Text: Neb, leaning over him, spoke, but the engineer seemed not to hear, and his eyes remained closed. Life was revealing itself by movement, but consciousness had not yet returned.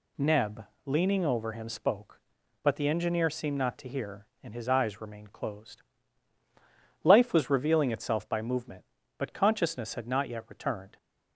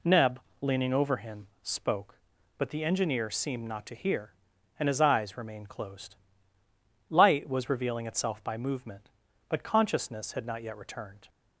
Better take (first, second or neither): first